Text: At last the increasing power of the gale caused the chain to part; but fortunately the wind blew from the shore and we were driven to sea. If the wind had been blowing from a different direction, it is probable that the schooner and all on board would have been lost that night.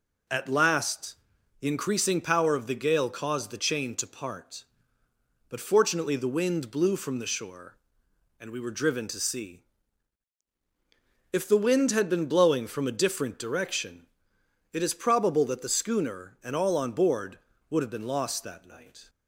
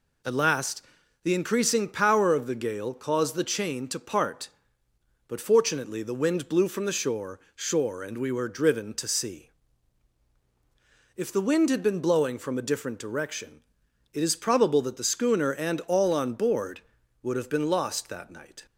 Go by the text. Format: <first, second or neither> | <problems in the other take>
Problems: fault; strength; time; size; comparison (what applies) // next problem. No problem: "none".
first | pauses between "last" and "the"; at 0.8 s; 0.42 s long; noticeable in the first // says "shore" twice; at 7.5 s